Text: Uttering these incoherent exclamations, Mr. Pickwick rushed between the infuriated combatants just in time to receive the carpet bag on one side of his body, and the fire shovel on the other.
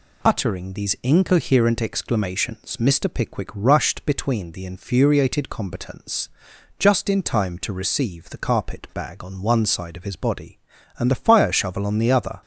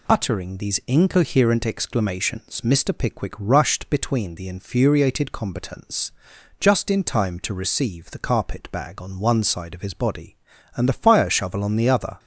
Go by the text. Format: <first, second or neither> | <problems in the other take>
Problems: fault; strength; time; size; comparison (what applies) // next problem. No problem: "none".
neither | pauses between "combatants" and "just"; noticeable; the same in both